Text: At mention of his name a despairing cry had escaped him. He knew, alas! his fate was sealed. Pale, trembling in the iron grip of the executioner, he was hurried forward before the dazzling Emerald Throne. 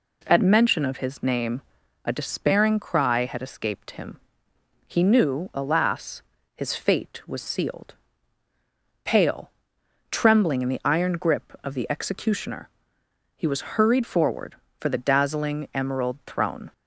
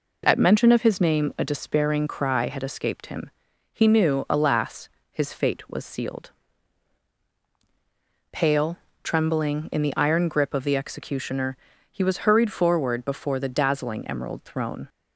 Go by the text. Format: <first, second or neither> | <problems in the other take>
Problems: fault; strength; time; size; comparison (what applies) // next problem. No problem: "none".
second | pauses between "name" and "a"; at 1.6 s; 0.42 s long // says "for" for "before"; at 14.7 s